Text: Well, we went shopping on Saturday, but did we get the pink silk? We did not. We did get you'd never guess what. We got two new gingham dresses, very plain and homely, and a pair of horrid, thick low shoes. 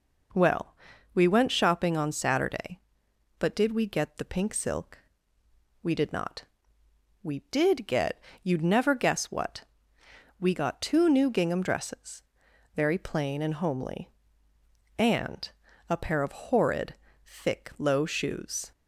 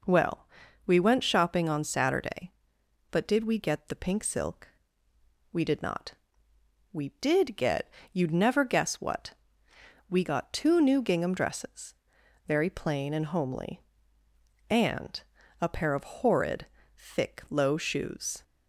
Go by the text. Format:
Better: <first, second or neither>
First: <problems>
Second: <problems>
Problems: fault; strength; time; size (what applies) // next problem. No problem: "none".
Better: neither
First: pauses between "get" and "you'd"; slight; at 8.1 s; 0.22 s long // pauses between "and" and "a"; at 15.4 s; 0.40 s long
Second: pauses between "get" and "you'd"; slight; at 7.8 s; 0.22 s long // pauses between "and" and "a"; at 15.2 s; 0.40 s long